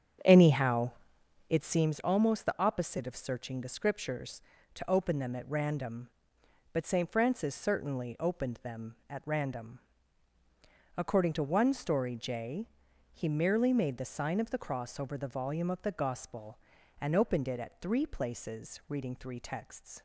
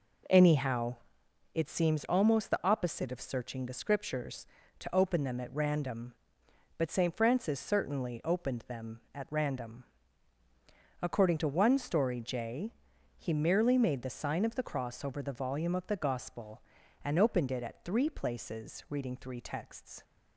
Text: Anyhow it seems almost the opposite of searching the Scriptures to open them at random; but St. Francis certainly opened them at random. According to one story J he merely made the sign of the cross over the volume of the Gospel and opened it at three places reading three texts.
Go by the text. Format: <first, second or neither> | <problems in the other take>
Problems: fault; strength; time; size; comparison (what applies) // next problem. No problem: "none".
second | starts louder than the rest; strong; until 1.9 s; 8 dB // pauses between "Anyhow" and "it"; noticeable; at 0.9 s; 0.58 s long; noticeable in the second // pauses between "J" and "he"; noticeable; at 12.6 s; 0.46 s long; noticeable in the second